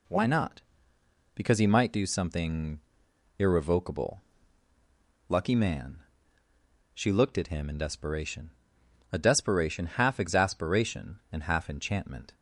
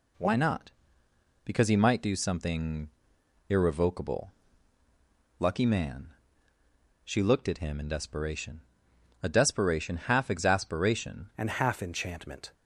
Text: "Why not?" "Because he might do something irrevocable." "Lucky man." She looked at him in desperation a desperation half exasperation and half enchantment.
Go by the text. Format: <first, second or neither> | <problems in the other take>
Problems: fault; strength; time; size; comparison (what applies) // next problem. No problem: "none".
first | pauses between "something" and "irrevocable"; noticeable; at 2.8 s; 0.60 s long; noticeable in the first // pauses between "desperation" and "a"; noticeable; at 8.6 s; 0.64 s long; noticeable in the first // changes voice at "and"; from 11.3 s on; 1.2 s long